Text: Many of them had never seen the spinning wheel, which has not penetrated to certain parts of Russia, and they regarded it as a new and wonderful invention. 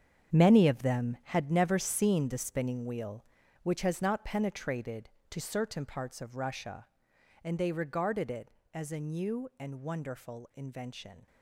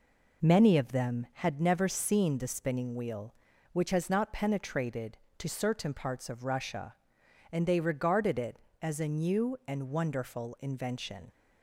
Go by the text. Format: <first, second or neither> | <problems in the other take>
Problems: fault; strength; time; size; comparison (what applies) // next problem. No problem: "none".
second | gets quieter; strong; throughout; 12 dB